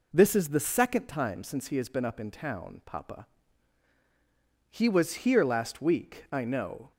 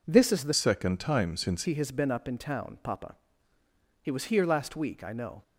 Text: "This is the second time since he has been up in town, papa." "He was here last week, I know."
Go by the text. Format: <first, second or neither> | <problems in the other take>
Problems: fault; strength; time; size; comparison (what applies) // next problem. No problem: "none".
first | changes voice from "second" to "since"; from 0.5 to 1.6 s; 1.1 s long